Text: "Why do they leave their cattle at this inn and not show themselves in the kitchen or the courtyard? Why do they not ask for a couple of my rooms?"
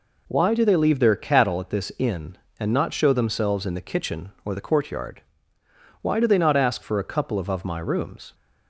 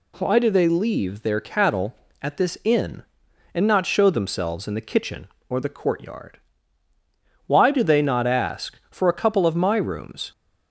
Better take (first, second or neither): second